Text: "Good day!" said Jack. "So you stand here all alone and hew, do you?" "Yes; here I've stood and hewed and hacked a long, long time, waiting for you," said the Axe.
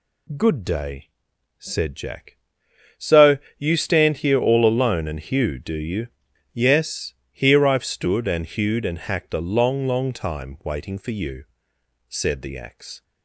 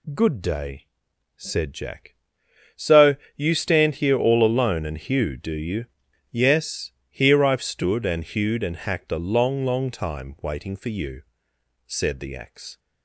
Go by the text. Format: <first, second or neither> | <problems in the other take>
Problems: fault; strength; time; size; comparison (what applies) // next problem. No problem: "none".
neither | pauses between "So" and "you"; slight; the same in both